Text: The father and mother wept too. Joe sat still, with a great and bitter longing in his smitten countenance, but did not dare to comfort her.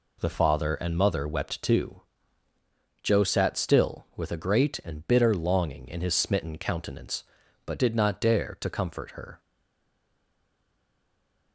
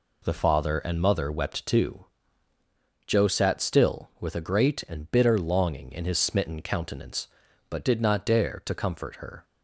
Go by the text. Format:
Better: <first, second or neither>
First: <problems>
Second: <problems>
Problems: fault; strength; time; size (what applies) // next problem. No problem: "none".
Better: second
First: stays silent after the last word; from 9.3 s on; 2.2 s long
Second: none